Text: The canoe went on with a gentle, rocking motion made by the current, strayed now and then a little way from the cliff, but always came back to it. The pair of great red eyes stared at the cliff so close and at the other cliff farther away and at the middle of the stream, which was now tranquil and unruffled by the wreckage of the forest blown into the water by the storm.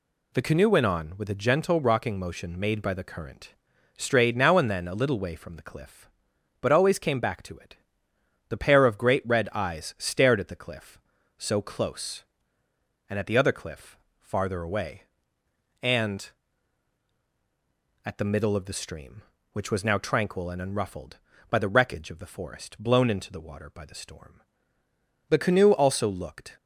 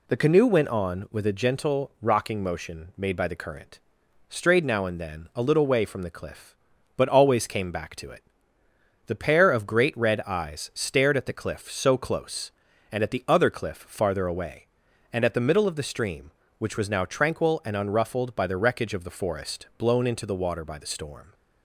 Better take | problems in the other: second | pauses between "cliff" and "farther"; slight; at 13.9 s; 0.20 s long // goes on to say "The canoe also looked"; noticeable; from 25.2 s on; 1.2 s long

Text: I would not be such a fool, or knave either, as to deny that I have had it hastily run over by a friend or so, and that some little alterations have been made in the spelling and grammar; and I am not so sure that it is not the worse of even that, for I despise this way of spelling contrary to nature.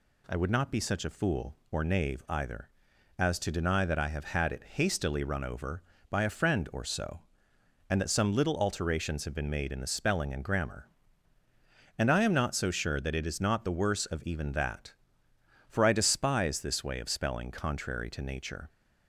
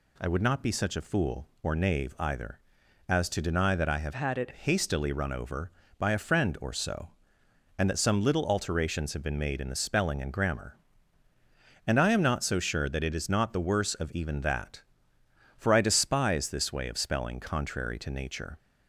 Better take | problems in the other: first | changes voice from "had" to "it"; from 4.1 to 4.5 s; 0.4 s long

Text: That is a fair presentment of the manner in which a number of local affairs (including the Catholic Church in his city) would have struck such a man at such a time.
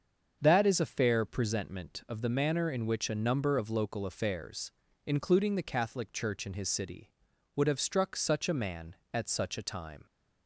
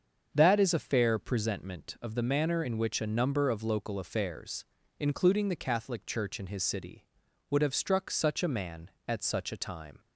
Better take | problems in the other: neither | starts louder than the rest; the same in both

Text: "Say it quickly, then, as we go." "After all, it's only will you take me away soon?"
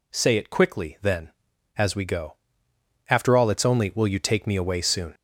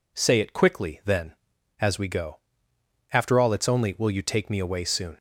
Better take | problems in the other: second | gets louder; throughout; 4 dB

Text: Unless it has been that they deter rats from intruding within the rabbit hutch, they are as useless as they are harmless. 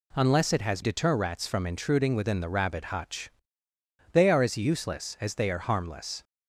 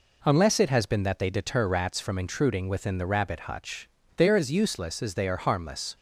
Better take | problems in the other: second | skips "been that they"; at 0.8 s

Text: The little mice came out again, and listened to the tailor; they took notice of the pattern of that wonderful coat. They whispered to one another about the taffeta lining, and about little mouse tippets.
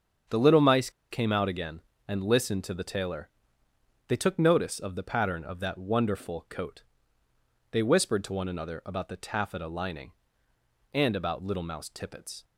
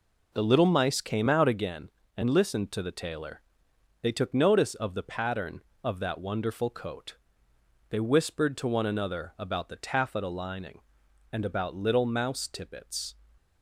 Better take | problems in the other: second | starts louder than the rest; strong; until 1.5 s; 7.5 dB // pauses between "mice" and "came"; slight; at 0.8 s; 0.21 s long

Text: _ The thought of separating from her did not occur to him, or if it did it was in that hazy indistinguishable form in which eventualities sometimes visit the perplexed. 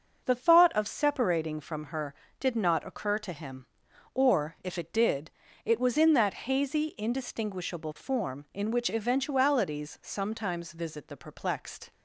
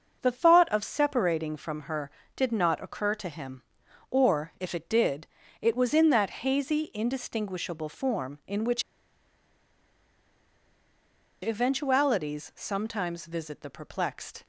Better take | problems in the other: first | starts louder than the rest; until 1.2 s; 6.5 dB; also in the first // pauses between "did" and "it"; slight; at 5.2 s; 0.34 s long; slight in the first // pauses between "which" and "eventualities"; strong; at 8.8 s; 2.6 s long

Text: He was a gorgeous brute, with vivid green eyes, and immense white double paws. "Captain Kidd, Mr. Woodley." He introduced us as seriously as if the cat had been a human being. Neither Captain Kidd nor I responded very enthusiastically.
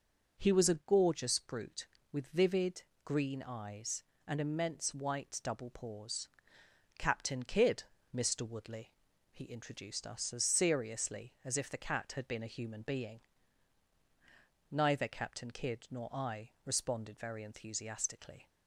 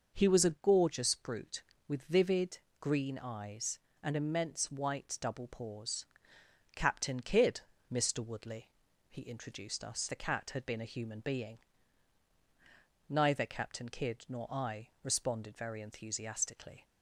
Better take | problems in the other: first | pauses between "vivid" and "green"; slight; at 2.5 s; 0.22 s long; slight in the first // skips "as seriously as if"; at 10.0 s

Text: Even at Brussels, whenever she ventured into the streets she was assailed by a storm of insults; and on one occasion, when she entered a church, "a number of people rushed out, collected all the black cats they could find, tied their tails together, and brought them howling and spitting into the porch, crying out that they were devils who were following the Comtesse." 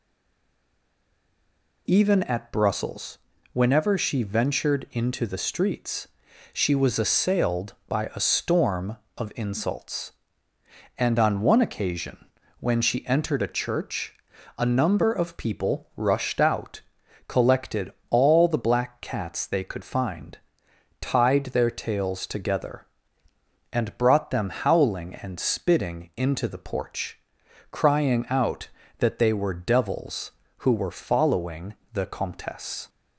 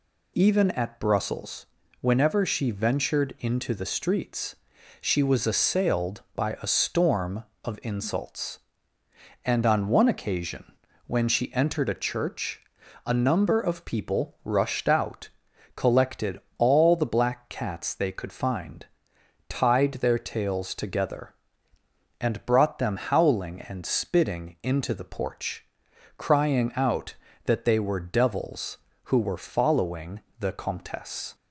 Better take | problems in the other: second | stays silent before the first word; noticeable; until 1.8 s; 1.8 s long // pauses between "streets" and "she"; at 6.0 s; 0.44 s long; also in the second // pauses between "collected" and "all"; slight; at 17.9 s; 0.16 s long; slight in the second // pauses between "following" and "the"; slight; at 31.7 s; 0.18 s long; slight in the second

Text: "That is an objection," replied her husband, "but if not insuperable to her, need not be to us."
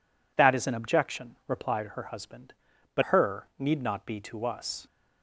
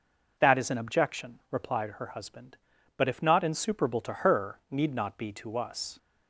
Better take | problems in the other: second | skips "if not insuperable to"; at 3.0 s

